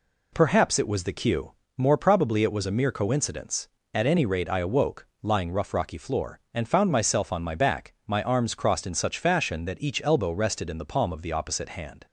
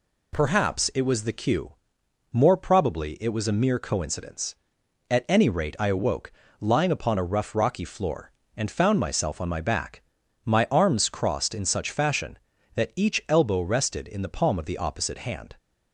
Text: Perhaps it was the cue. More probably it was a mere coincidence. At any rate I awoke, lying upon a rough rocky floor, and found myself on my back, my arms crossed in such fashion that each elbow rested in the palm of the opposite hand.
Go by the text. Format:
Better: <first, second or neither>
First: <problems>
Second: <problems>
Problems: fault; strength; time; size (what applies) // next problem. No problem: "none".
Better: second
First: skips "upon a"; at 5.5 s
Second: none